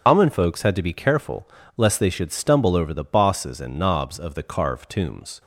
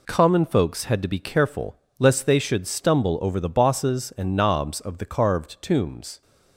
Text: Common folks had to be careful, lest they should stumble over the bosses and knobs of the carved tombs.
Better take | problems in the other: second | loses the start of "Common"; at 0.0 s; 100 ms // starts louder than the rest; strong; until 1.0 s; 7.5 dB

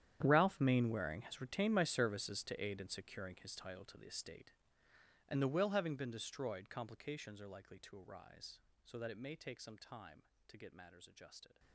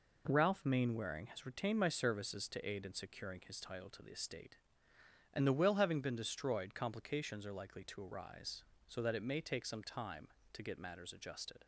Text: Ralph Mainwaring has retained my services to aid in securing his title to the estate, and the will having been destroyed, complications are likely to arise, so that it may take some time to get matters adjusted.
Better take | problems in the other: second | gets quieter; strong; throughout; 18 dB

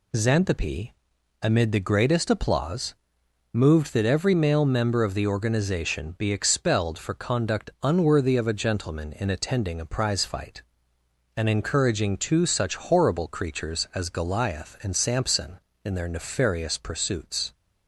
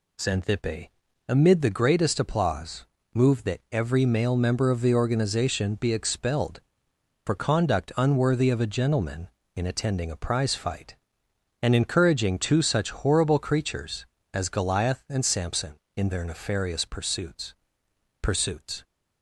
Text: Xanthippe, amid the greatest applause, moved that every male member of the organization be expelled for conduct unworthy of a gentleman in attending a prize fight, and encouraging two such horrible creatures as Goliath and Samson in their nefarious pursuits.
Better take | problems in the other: first | says "pursuits" twice; at 18.1 s

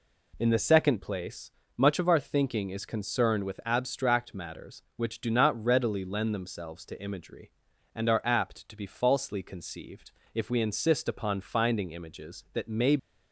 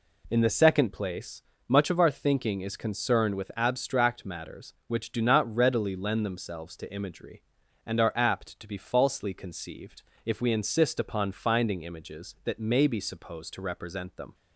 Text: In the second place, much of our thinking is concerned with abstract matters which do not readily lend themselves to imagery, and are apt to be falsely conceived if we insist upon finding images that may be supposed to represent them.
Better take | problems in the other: second | pauses between "conceived" and "if"; slight; at 10.1 s; 0.22 s long; slight in the second // stops before "be supposed to represent them"; at 12.9 s

